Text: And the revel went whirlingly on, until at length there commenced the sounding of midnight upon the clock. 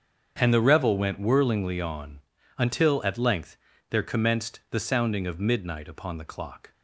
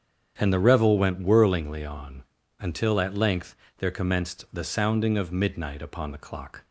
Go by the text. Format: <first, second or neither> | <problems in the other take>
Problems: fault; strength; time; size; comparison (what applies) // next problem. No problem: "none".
neither | starts louder than the rest; strong; the same in both // pauses between "length" and "there"; slight; the same in both